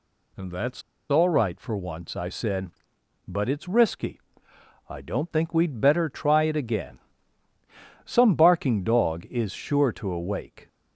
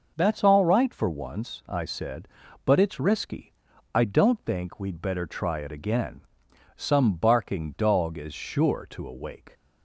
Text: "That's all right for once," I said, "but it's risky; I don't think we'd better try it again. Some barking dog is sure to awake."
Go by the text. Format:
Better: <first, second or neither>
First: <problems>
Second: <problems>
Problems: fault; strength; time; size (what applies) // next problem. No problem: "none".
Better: second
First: pauses between "That's" and "all"; slight; at 0.8 s; 0.28 s long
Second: none